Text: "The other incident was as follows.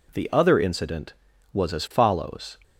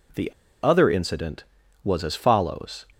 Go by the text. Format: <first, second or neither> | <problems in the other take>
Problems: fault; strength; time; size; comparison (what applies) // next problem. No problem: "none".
first | pauses between "The" and "other"; slight; at 0.2 s; 0.34 s long